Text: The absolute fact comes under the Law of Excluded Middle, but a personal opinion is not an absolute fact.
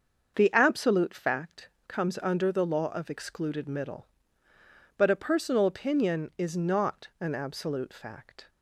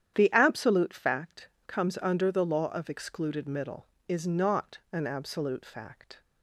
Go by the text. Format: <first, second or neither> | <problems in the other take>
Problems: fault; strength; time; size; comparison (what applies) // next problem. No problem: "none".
first | starts louder than the rest; strong; until 1.1 s; 10 dB; also in the first // pauses between "fact" and "comes"; slight; at 1.4 s; 0.18 s long; slight in the first // skips "but a personal opinion"; at 3.9 s